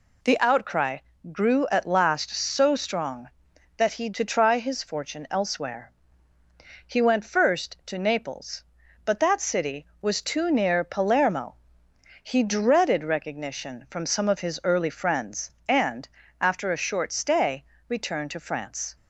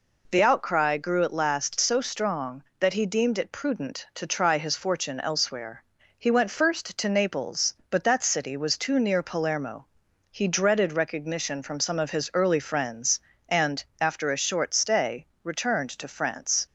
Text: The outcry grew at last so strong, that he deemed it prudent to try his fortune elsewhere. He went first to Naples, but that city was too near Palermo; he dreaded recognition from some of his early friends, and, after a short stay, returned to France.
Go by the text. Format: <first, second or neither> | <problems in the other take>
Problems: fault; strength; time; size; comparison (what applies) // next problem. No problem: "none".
second | pauses between "outcry" and "grew"; slight; at 0.9 s; 0.34 s long // skips "deemed it prudent"; at 4.0 s